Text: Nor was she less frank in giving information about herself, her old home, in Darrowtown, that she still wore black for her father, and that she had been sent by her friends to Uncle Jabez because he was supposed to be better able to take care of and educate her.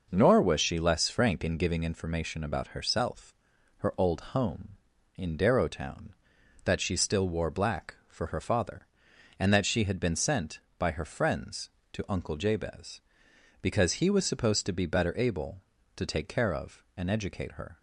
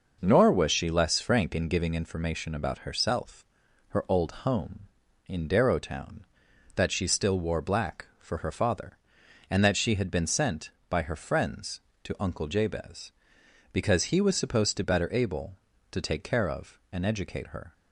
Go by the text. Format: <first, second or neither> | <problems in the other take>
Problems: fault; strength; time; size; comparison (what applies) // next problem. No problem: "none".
first | skips "be"; at 14.8 s